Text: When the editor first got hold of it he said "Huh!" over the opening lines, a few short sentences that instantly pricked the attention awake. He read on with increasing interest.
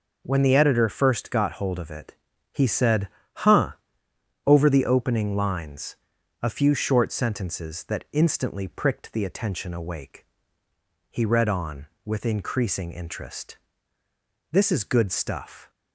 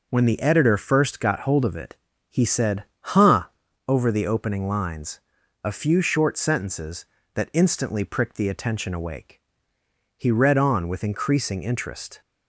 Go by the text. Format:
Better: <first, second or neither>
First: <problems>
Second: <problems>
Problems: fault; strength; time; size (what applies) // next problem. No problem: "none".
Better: second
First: pauses between "it" and "he"; at 2.1 s; 0.38 s long // pauses between "said" and "Huh"; slight; at 3.0 s; 0.26 s long // goes on to say "This is good stuff"; noticeable; from 14.5 s on; 1.1 s long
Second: pauses between "it" and "he"; slight; at 1.9 s; 0.34 s long // pauses between "said" and "Huh"; slight; at 2.8 s; 0.16 s long